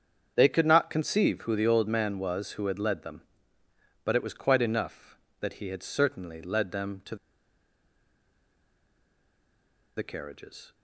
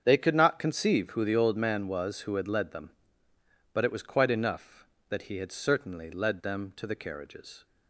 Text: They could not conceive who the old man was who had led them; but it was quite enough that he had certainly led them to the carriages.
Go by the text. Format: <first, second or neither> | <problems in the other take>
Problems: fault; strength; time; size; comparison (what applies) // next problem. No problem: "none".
second | starts louder than the rest; strong; until 1.3 s; 7.5 dB; strong in the second // pauses between "to" and "the"; strong; at 7.1 s; 2.8 s long